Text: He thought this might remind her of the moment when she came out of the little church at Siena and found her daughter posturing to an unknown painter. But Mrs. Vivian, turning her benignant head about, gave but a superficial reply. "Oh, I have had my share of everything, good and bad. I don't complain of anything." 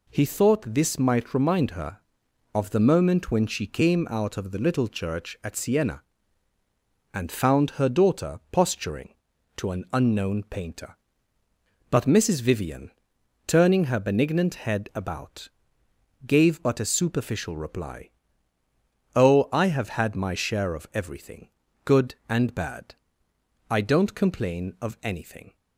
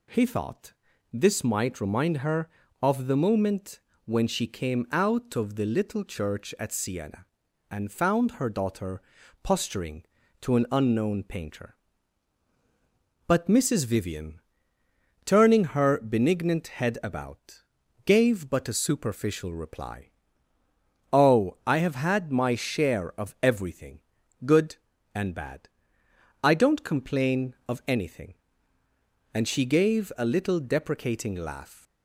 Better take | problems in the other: first | pauses between "thought" and "this"; at 0.7 s; 0.40 s long // pauses between "moment" and "when"; slight; at 3.7 s; 0.26 s long // pauses between "daughter" and "posturing"; at 9.0 s; 0.42 s long // goes on to say "And she gave a little deprecating laugh"; strong; from 29.3 s on; 2.5 s long

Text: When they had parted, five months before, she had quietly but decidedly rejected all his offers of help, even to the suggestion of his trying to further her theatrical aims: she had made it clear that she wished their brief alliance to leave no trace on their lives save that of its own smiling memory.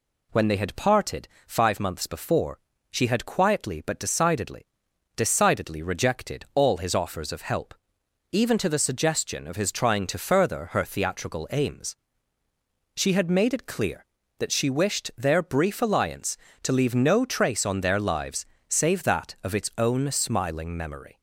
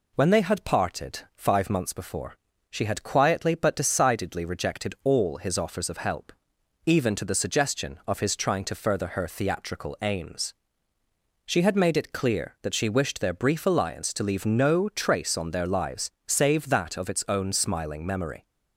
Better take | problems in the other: second | says "decidedly" twice; at 5.1 s // pauses between "lives" and "save"; slight; at 18.4 s; 0.22 s long; slight in the second

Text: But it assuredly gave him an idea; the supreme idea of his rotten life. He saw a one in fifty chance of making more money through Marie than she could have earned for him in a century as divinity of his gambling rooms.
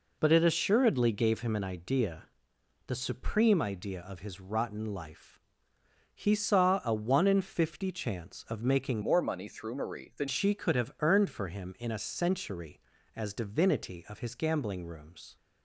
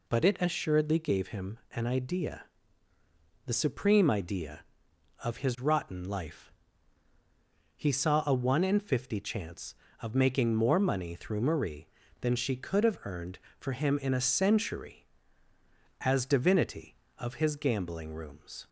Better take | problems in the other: second | changes voice from "more" to "than"; from 9.0 to 10.2 s; 1.2 s long

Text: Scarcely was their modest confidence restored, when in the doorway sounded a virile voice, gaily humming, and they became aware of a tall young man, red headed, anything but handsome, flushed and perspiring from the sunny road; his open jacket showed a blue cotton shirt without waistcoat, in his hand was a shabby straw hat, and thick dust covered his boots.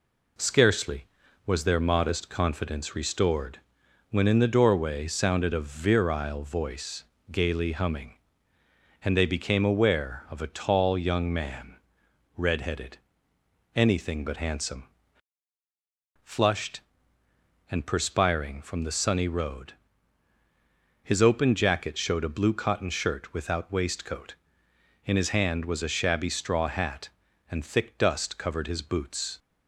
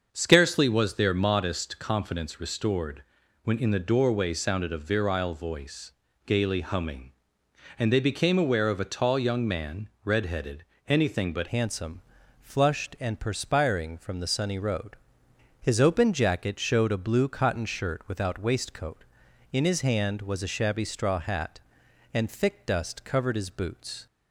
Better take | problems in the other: first | starts louder than the rest; until 1.1 s; 6.5 dB // changes voice at "handsome"; from 11.4 s on; 12.6 s long

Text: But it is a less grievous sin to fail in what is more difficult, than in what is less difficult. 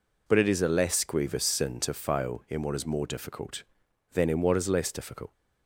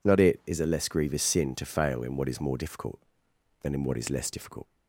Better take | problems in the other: first | says "Not" for "But"; at 0.0 s

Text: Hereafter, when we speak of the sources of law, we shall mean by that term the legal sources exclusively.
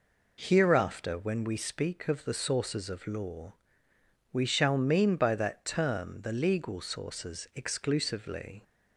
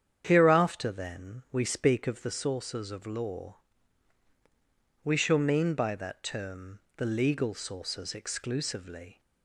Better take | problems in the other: first | starts louder than the rest; strong; until 1.2 s; 8.5 dB // says "then" for "when"; at 0.9 s // pauses between "term" and "the"; slight; at 6.7 s; 0.16 s long

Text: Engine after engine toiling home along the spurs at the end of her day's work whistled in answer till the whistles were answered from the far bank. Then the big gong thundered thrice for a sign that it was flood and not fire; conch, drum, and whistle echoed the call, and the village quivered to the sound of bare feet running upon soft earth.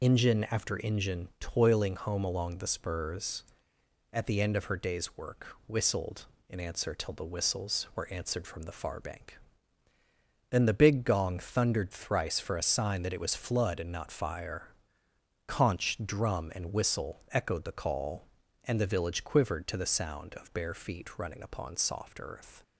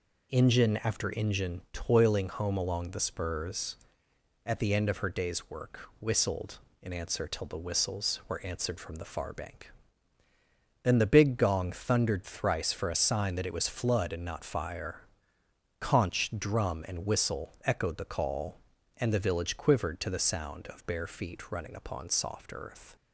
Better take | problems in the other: second | loses the start of "Engine"; at 0.0 s; 35 ms

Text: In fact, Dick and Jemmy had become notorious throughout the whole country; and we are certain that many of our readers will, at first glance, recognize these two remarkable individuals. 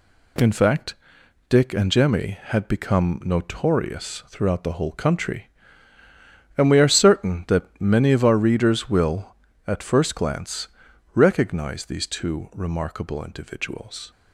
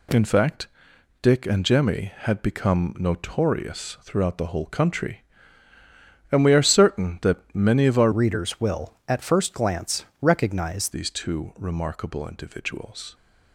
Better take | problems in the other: first | changes voice from "readers" to "recognize"; from 8.1 to 10.8 s; 2.7 s long

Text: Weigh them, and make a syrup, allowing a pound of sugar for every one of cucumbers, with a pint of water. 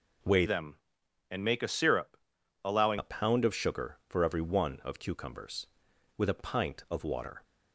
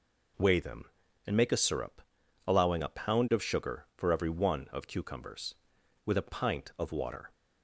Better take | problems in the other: second | changes voice from "them" to "allowing"; from 0.4 to 2.9 s; 2.5 s long

